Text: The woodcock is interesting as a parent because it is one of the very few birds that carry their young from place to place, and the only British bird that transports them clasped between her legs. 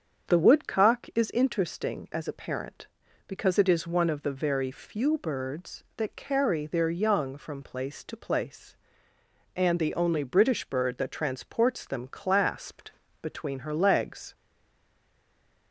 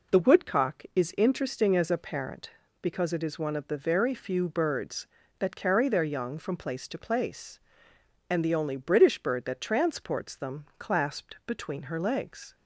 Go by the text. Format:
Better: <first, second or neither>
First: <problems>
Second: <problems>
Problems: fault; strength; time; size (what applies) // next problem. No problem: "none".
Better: second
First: starts louder than the rest; strong; until 1.3 s; 7 dB // pauses between "clasped" and "between"; slight; at 12.9 s; 0.30 s long // stays silent after the last word; noticeable; from 14.3 s on; 1.4 s long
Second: none